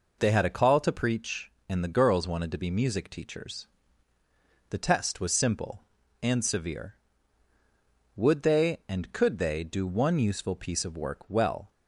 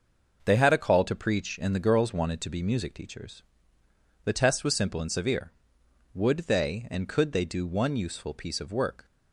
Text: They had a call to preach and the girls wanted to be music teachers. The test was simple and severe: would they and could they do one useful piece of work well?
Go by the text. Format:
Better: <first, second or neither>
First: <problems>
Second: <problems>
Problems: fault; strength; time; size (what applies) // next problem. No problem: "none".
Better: first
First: none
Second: starts louder than the rest; noticeable; until 1.4 s; 6 dB // stops before "well"; at 9.0 s